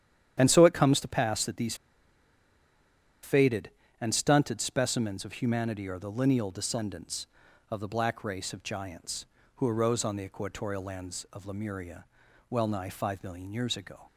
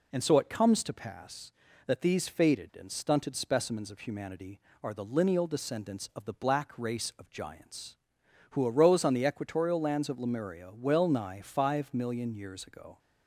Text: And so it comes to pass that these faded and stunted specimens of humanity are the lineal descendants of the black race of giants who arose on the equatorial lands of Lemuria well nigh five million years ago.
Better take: second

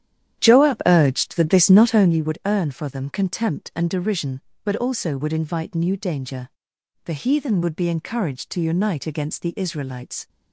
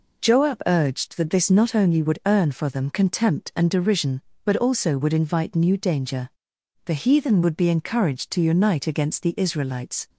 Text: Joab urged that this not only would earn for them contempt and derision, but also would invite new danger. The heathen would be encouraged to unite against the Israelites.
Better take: second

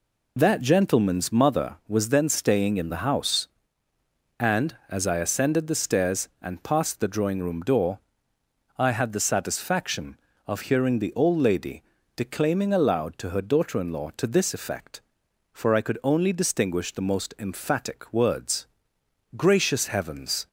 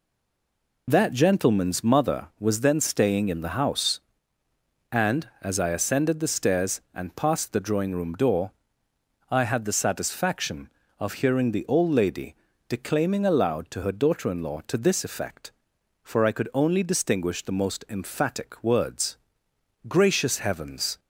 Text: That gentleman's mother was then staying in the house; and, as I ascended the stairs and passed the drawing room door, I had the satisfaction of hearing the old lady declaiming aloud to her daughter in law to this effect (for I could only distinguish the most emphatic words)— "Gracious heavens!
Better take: first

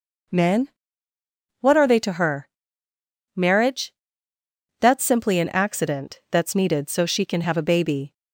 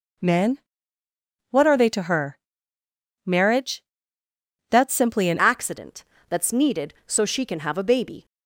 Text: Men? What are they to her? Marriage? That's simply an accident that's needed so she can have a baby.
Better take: first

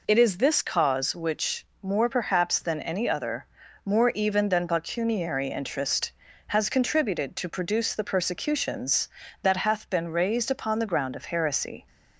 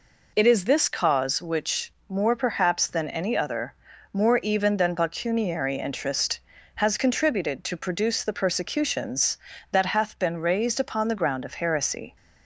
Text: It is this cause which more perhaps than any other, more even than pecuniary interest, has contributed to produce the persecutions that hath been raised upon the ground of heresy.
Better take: neither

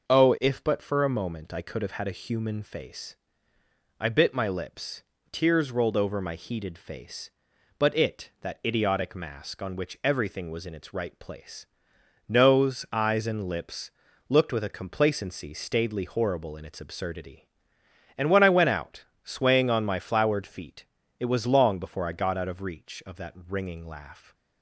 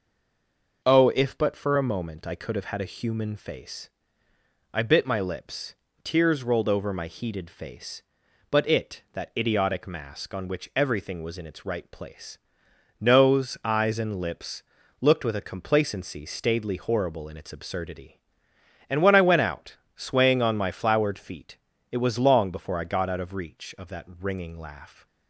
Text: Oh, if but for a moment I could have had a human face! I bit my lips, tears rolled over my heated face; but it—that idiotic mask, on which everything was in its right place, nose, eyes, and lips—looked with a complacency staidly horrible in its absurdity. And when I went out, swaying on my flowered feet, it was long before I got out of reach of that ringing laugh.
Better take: first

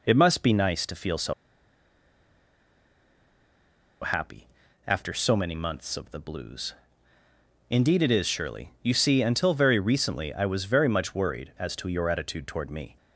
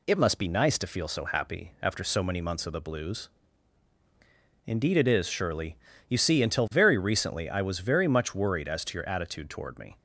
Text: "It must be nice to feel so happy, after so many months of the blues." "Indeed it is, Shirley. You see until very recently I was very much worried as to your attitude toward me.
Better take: second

